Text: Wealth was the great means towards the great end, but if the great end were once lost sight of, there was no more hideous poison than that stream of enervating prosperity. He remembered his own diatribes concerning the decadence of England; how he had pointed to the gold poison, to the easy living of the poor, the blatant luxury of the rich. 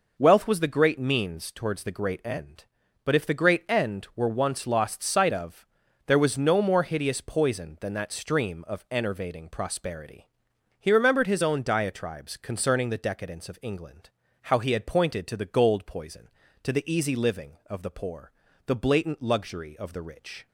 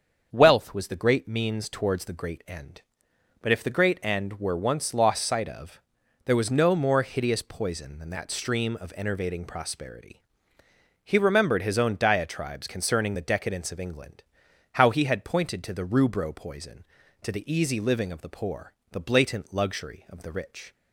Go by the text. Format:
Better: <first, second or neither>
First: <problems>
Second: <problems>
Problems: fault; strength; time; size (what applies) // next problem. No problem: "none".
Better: first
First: none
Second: starts louder than the rest; until 1.3 s; 7 dB // says "rubro" for "gold"; at 15.8 s